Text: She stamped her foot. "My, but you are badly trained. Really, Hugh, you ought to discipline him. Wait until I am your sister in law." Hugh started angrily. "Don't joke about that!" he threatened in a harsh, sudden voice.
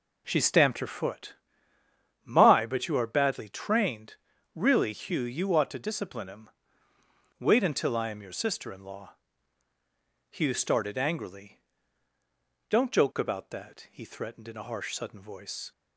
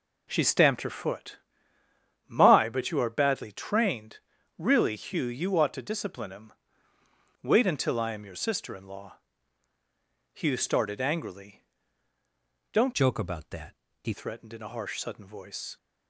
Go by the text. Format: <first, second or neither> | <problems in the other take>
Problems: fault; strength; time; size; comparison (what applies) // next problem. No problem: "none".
first | changes voice from "joke" to "he"; from 12.9 to 14.1 s; 1.2 s long